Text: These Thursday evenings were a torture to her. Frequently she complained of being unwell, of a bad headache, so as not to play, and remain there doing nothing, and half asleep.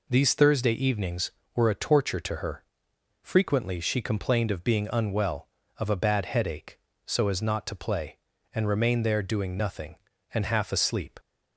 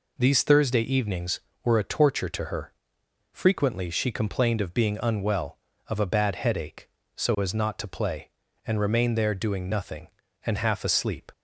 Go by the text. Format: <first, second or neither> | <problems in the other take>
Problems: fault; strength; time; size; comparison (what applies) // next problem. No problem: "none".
neither | none